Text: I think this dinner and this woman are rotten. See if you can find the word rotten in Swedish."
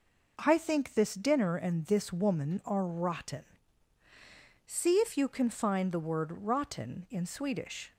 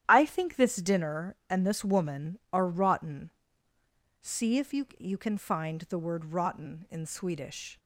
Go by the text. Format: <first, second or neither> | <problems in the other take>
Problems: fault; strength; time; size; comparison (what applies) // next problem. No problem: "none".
first | starts louder than the rest; strong; until 1.0 s; 11 dB // says "you" twice; at 4.9 s